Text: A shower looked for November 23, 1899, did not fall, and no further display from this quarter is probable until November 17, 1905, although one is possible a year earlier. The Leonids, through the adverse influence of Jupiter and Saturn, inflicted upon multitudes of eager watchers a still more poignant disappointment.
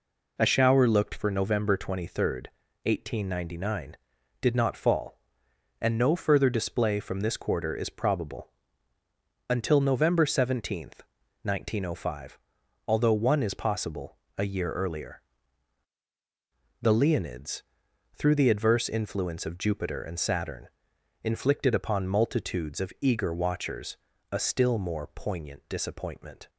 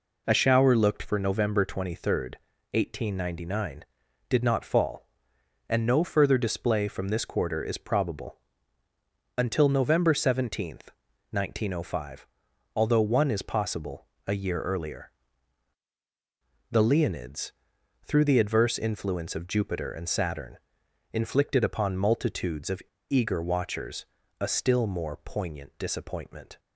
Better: first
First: pauses between "probable" and "until"; at 8.4 s; 1.0 s long // pauses between "possible" and "a"; slight; at 14.1 s; 0.20 s long // pauses between "watchers" and "a"; slight; at 23.9 s; 0.34 s long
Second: pauses between "probable" and "until"; at 8.3 s; 1.0 s long // pauses between "possible" and "a"; slight; at 14.0 s; 0.20 s long // pauses between "of" and "eager"; slight; at 22.8 s; 0.27 s long // pauses between "watchers" and "a"; slight; at 24.0 s; 0.34 s long

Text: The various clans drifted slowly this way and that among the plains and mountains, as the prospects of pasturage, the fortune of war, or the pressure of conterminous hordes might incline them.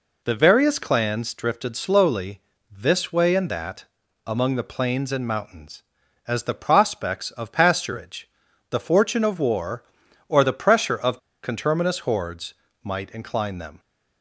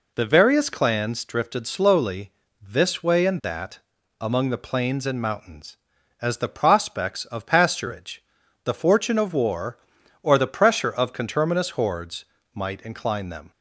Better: second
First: pauses between "slowly" and "this"; slight; at 2.4 s; 0.30 s long // pauses between "that" and "among"; at 3.8 s; 0.38 s long // pauses between "of" and "conterminous"; slight; at 11.1 s; 0.24 s long // pauses between "hordes" and "might"; slight; at 12.5 s; 0.30 s long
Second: pauses between "slowly" and "this"; slight; at 2.3 s; 0.30 s long // pauses between "that" and "among"; at 3.8 s; 0.38 s long // pauses between "hordes" and "might"; slight; at 12.2 s; 0.30 s long

